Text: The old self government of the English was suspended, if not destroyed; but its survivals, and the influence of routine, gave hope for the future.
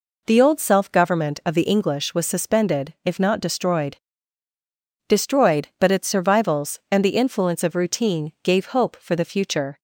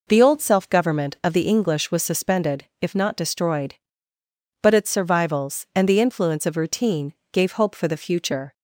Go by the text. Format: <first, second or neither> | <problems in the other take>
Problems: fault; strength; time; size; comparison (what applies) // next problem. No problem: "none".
second | says "destroyed" twice; at 5.0 s